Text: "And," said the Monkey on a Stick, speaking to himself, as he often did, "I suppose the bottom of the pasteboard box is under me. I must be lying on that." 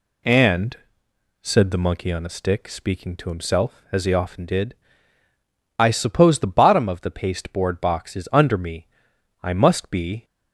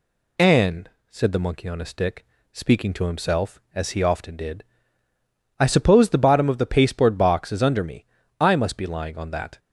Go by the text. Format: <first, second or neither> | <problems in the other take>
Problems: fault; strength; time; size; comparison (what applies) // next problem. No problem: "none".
second | stops before "lying on that"; at 10.2 s